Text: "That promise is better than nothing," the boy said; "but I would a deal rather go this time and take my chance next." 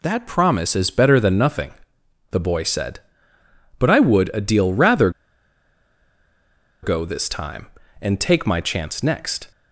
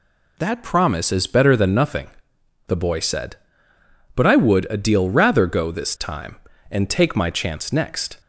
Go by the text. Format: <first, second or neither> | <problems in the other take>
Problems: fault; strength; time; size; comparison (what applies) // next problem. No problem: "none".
second | pauses between "rather" and "go"; strong; at 5.1 s; 1.7 s long